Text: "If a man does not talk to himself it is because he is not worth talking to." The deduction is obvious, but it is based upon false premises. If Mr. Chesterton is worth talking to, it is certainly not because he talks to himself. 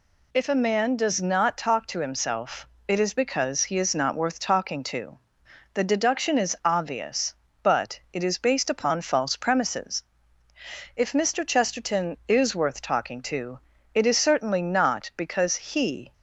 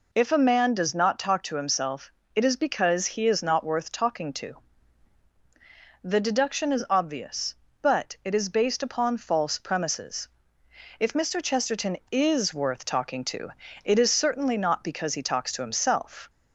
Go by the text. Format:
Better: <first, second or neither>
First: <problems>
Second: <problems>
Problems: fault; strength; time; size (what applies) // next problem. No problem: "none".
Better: second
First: pauses between "himself" and "it"; slight; at 2.6 s; 0.22 s long // stops before "talks to himself"; at 16.1 s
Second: pauses between "himself" and "it"; slight; at 2.1 s; 0.24 s long